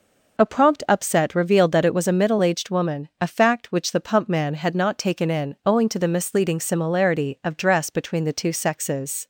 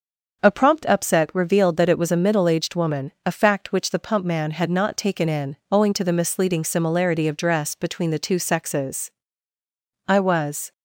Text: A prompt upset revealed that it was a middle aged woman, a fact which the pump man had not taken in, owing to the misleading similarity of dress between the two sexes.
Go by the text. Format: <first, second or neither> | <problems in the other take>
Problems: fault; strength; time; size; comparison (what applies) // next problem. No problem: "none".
first | starts louder than the rest; until 1.4 s; 6.5 dB // goes on to say "I was"; noticeable; from 10.0 s on; 0.64 s long